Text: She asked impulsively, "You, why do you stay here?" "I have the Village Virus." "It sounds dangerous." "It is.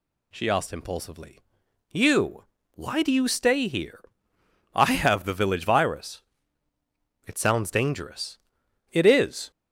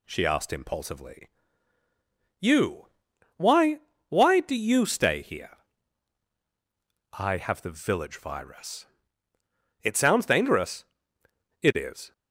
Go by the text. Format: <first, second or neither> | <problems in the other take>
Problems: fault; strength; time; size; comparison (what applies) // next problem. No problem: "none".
first | says "why" twice; at 4.0 s